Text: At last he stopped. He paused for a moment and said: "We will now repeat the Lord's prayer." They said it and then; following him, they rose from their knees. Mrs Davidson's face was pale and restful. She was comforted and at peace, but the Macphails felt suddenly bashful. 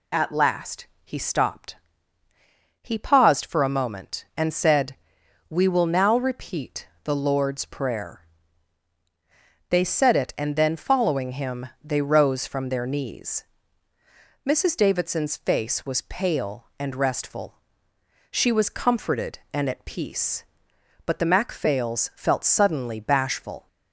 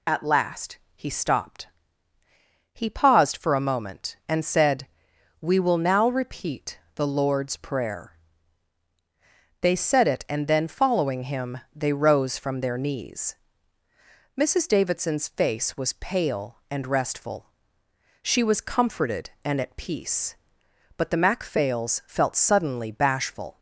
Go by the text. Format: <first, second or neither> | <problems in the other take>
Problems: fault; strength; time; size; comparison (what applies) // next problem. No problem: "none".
first | loses the start of "At"; at 0.0 s; 35 ms // pauses between "last" and "he"; slight; at 0.7 s; 0.18 s long; slight in the first // pauses between "repeat" and "the"; slight; at 6.7 s; 0.16 s long; slight in the first